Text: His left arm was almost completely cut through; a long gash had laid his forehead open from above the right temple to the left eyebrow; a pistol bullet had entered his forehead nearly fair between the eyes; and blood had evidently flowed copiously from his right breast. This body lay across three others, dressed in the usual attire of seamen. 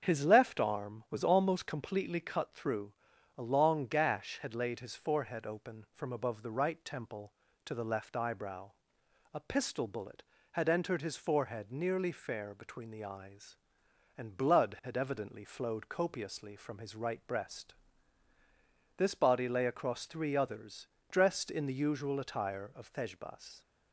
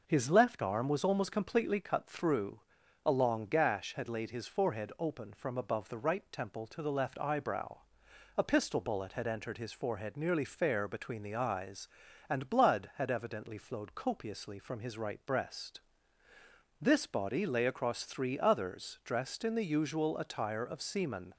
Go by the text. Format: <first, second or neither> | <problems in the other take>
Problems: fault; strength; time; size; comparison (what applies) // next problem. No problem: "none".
second | starts louder than the rest; until 1.0 s; 7 dB // says "thejbas" for "seamen"; at 22.8 s